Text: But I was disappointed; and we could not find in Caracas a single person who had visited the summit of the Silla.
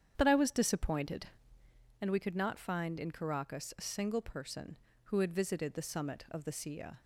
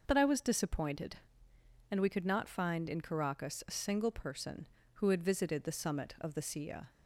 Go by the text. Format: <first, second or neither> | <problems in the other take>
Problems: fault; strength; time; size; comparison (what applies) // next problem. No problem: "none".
second | starts louder than the rest; strong; until 1.9 s; 8.5 dB